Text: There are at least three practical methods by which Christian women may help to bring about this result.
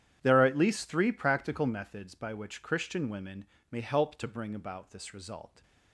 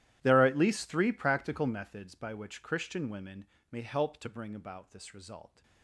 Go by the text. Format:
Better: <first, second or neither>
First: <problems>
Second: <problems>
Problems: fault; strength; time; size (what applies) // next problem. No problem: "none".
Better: first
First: starts louder than the rest; strong; until 1.2 s; 10 dB // pauses between "women" and "may"; slight; at 3.4 s; 0.26 s long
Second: gets quieter; strong; throughout; 21 dB // starts louder than the rest; strong; until 1.2 s; 13 dB // pauses between "women" and "may"; slight; at 3.4 s; 0.26 s long